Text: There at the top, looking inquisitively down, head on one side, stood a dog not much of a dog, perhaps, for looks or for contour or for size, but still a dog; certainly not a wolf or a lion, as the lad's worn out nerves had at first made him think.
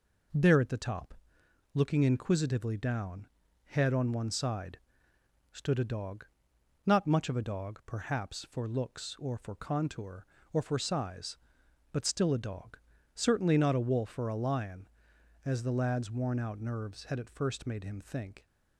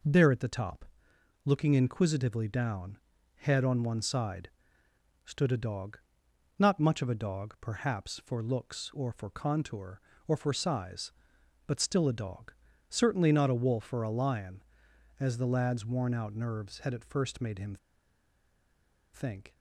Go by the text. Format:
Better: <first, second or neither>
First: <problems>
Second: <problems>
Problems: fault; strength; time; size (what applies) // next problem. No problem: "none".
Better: first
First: pauses between "dog" and "not"; noticeable; at 6.2 s; 0.60 s long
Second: pauses between "dog" and "not"; noticeable; at 5.9 s; 0.60 s long // pauses between "him" and "think"; strong; at 17.7 s; 1.3 s long